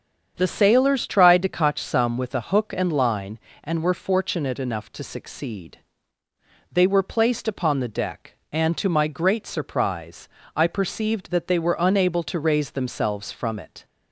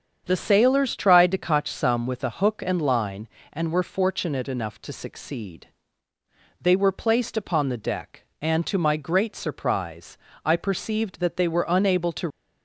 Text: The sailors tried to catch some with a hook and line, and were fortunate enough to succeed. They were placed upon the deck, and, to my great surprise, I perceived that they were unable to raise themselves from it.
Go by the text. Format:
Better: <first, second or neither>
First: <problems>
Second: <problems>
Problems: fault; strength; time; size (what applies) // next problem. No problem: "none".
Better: first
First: starts louder than the rest; strong; until 1.3 s; 7.5 dB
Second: starts louder than the rest; strong; until 1.2 s; 7.5 dB // stops before "raise themselves from it"; at 12.2 s